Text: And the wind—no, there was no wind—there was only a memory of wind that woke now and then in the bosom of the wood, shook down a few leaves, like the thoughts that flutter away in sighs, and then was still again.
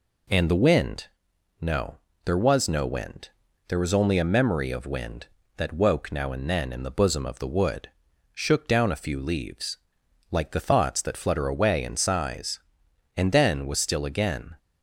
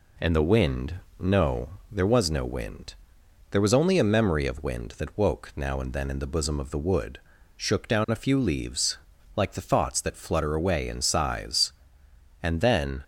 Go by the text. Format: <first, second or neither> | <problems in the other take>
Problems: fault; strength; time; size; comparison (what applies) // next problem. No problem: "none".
first | stops before "was still again"; at 13.0 s